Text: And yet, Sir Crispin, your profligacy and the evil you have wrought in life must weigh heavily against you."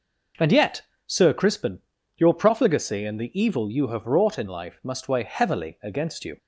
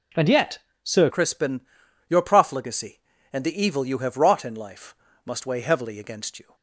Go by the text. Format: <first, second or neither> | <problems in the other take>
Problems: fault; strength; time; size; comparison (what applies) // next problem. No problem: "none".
first | changes voice at "Crispin"; from 1.1 s on; 5.4 s long // pauses between "life" and "must"; slight; at 4.9 s; 0.30 s long